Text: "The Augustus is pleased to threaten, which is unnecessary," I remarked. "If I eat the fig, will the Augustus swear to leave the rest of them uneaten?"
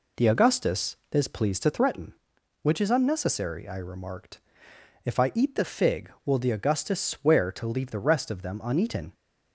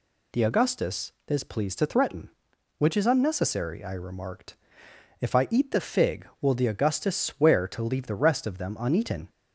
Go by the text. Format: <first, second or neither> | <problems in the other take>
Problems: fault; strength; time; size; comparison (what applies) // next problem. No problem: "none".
second | starts louder than the rest; slight; until 1.8 s; 3.5 dB